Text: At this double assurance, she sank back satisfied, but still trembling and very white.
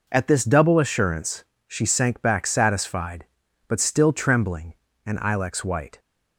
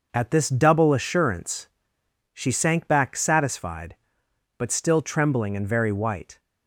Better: second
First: says "ilex" for "very"; at 5.1 s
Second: none

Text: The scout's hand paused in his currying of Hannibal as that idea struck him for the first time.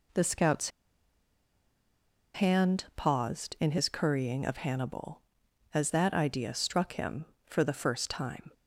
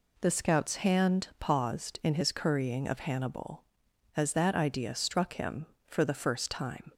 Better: second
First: pauses between "scout's" and "hand"; strong; at 0.7 s; 1.6 s long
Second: none

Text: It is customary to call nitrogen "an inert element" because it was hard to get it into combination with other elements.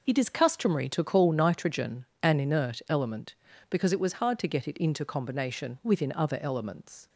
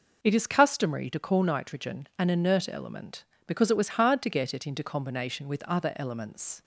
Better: second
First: pauses between "nitrogen" and "an"; slight; at 2.0 s; 0.16 s long // says "within" for "with"; at 5.8 s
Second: none

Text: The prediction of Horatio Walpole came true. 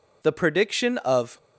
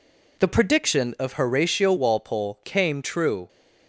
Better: second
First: stops before "Horatio Walpole came true"; at 1.3 s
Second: none

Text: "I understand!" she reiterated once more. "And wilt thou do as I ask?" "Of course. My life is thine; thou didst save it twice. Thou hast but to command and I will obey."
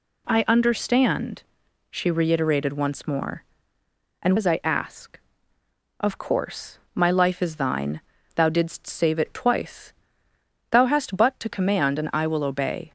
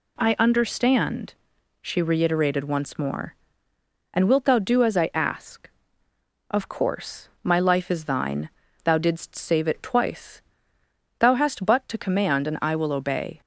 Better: second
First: skips "wilt thou do"; at 4.3 s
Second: none

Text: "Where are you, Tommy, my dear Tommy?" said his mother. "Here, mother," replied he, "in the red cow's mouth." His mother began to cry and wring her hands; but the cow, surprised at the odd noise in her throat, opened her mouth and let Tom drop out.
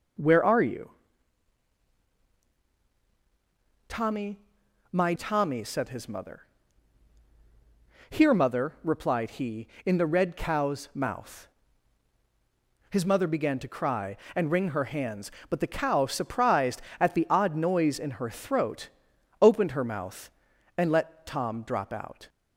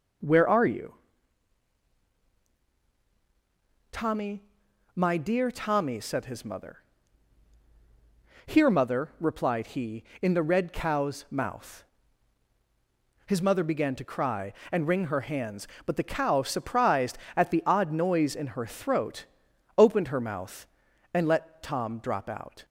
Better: second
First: skips "dear"; at 5.1 s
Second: none

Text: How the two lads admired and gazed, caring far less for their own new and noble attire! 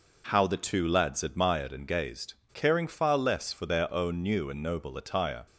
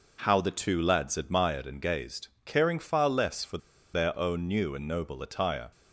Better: first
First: none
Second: pauses between "for" and "their"; at 3.5 s; 0.36 s long

